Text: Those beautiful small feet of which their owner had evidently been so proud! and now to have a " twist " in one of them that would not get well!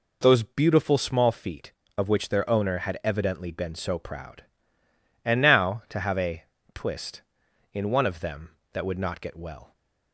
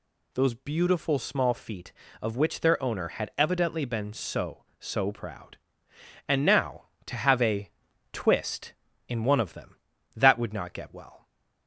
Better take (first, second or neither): first